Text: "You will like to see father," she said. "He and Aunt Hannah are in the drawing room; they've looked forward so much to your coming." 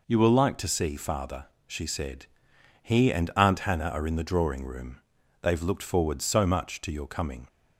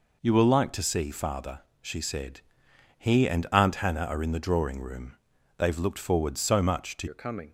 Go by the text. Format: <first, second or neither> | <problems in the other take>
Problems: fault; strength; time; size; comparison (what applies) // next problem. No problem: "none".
first | changes voice at "your"; from 7.0 s on; 0.5 s long